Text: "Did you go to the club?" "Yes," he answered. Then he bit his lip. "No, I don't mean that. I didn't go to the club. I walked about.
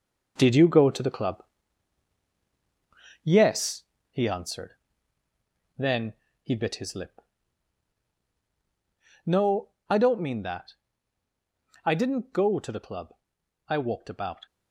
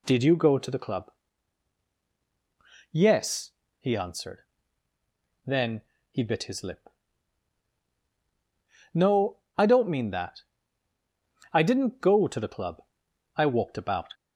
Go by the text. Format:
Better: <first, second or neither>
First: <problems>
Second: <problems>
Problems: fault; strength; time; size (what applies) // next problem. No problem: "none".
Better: second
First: gets quieter; strong; throughout; 8 dB // pauses between "Then" and "he"; slight; at 6.1 s; 0.30 s long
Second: pauses between "Then" and "he"; slight; at 5.7 s; 0.30 s long